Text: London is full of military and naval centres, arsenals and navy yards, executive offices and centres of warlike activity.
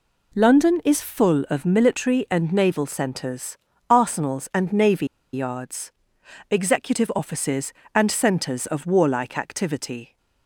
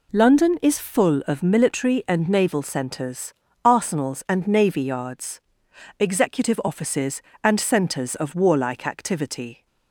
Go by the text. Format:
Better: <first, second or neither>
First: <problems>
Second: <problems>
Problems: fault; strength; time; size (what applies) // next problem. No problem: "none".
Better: second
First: pauses between "navy" and "yards"; slight; at 5.0 s; 0.28 s long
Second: none